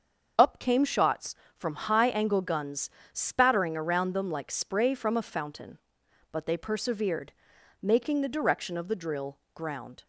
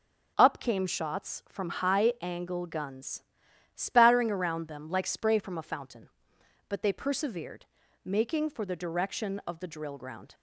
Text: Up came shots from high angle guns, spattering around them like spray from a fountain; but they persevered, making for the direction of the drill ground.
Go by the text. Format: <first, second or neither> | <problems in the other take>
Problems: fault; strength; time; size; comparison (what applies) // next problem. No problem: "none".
second | starts louder than the rest; until 1.5 s; 6.5 dB // skips "for"; at 8.2 s // pauses between "drill" and "ground"; slight; at 9.3 s; 0.16 s long